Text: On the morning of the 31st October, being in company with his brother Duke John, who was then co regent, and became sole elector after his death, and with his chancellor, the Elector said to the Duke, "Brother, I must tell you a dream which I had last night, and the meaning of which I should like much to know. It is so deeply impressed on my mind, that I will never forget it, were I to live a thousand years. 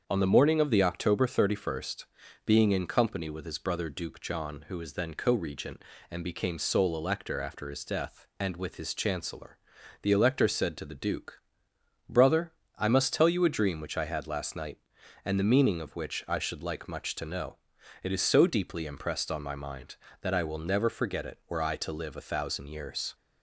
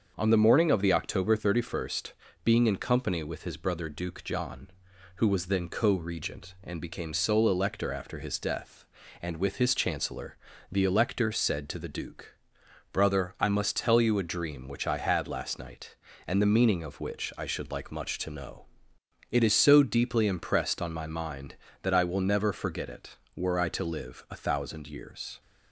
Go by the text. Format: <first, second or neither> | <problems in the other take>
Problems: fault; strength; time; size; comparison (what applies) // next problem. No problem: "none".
neither | starts louder than the rest; the same in both